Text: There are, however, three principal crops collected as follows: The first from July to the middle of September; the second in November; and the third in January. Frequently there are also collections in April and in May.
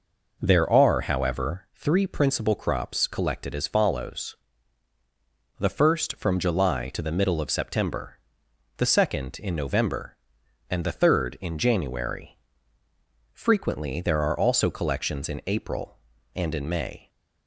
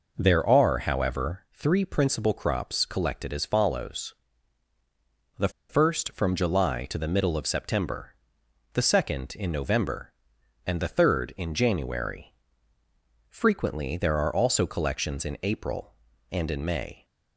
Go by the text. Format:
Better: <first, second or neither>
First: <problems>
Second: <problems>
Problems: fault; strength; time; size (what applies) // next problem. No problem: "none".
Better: first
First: none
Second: pauses between "The" and "first"; slight; at 5.4 s; 0.19 s long